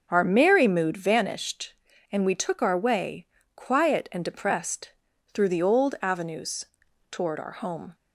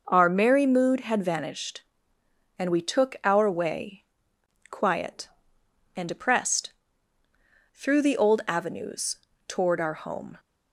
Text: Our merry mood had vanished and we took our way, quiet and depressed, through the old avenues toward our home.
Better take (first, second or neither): second